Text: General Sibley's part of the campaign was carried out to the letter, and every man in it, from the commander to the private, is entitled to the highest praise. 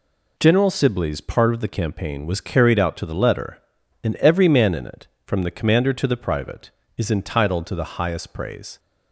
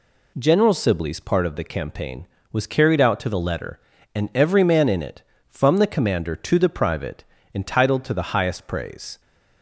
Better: first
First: none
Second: skips "is"; at 7.3 s

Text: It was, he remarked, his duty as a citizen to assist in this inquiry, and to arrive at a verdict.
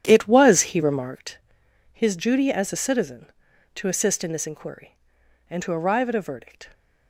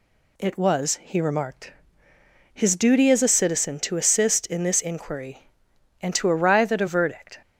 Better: second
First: starts louder than the rest; strong; until 1.3 s; 10 dB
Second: none

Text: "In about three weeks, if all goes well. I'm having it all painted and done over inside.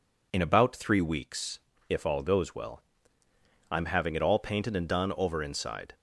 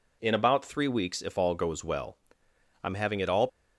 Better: first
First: none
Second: stops before "painted and done over inside"; at 3.4 s

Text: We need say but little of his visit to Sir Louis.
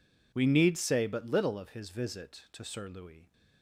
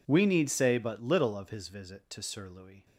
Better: neither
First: none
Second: none

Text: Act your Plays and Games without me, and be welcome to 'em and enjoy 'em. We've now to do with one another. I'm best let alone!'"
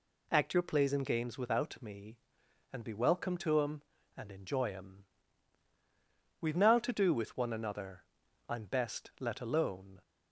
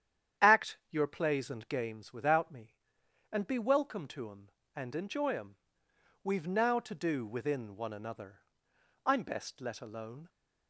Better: first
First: none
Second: starts louder than the rest; strong; until 1.5 s; 9.5 dB // says "within" for "with"; at 7.2 s

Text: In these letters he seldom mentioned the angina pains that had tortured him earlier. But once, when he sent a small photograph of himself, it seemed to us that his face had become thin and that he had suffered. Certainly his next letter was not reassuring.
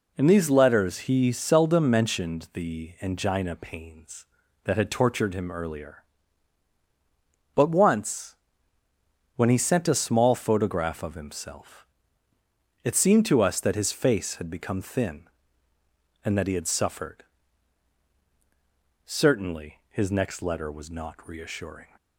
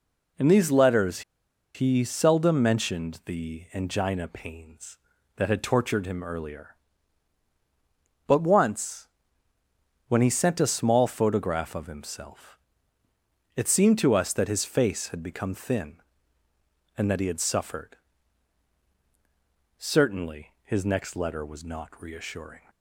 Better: first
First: none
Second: pauses between "letters" and "he"; noticeable; at 1.2 s; 0.53 s long

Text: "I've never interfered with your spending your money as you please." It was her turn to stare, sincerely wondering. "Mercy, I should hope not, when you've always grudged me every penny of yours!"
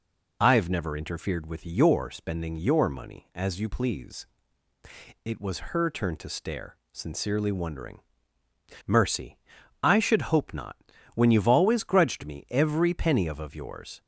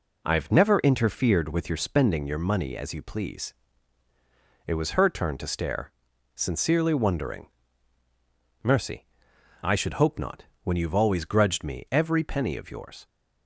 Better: second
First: says "of" twice; at 13.3 s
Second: none

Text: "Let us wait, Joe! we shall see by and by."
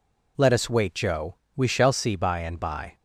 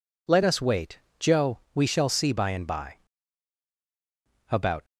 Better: first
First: none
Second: goes on to say "About"; slight; from 4.5 s on; 0.32 s long

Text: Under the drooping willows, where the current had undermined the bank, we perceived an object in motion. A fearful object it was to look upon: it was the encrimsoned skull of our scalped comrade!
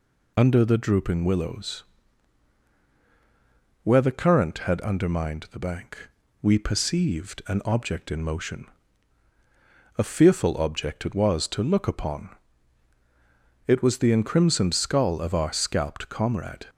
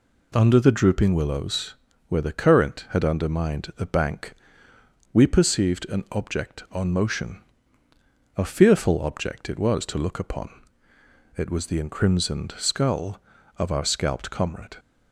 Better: first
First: none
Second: says "on" for "in"; at 6.7 s

